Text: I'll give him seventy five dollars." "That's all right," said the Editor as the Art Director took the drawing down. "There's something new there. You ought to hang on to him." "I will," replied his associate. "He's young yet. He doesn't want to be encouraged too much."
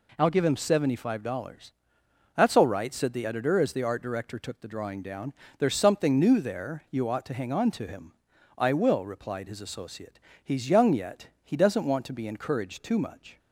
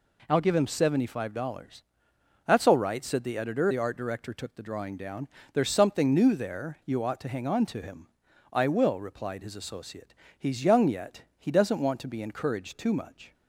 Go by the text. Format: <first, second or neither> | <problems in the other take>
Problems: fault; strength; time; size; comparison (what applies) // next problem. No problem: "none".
first | skips "as"; at 3.7 s